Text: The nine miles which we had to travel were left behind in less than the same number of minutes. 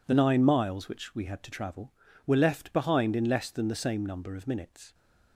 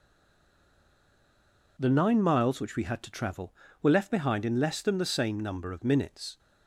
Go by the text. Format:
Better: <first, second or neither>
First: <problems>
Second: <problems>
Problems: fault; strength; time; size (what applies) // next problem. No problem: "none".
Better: first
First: none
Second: stays silent before the first word; noticeable; until 1.7 s; 1.7 s long